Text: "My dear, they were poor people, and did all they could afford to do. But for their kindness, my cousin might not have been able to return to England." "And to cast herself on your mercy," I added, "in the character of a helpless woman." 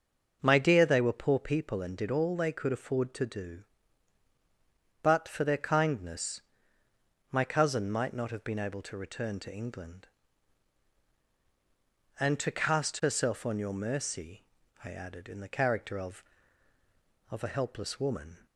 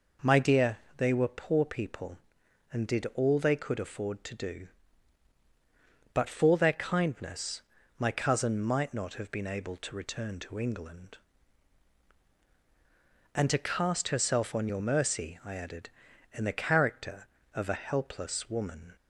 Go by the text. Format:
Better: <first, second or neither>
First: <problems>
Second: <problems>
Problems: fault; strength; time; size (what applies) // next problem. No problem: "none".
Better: second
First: starts louder than the rest; noticeable; until 1.4 s; 6 dB // says "of" twice; at 17.2 s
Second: none